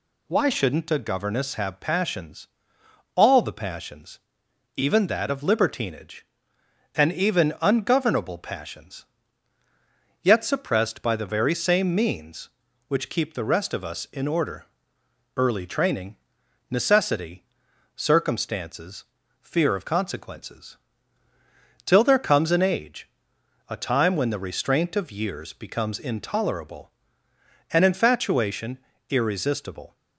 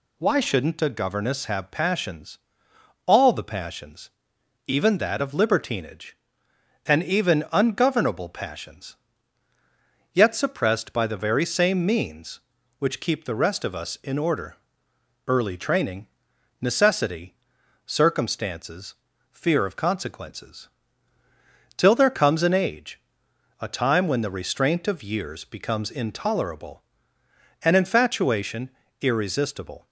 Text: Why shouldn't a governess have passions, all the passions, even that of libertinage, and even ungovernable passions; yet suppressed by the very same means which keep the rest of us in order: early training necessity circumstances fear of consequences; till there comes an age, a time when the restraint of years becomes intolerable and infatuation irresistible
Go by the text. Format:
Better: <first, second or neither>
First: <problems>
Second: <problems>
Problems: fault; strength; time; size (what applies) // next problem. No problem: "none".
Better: neither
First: pauses between "training" and "necessity"; noticeable; at 16.1 s; 0.54 s long // pauses between "necessity" and "circumstances"; noticeable; at 17.4 s; 0.50 s long // pauses between "circumstances" and "fear"; slight; at 19.0 s; 0.36 s long // pauses between "infatuation" and "irresistible"; slight; at 28.7 s; 0.32 s long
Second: pauses between "training" and "necessity"; noticeable; at 16.0 s; 0.54 s long // pauses between "necessity" and "circumstances"; noticeable; at 17.3 s; 0.49 s long // pauses between "circumstances" and "fear"; slight; at 18.9 s; 0.36 s long // pauses between "infatuation" and "irresistible"; slight; at 28.7 s; 0.32 s long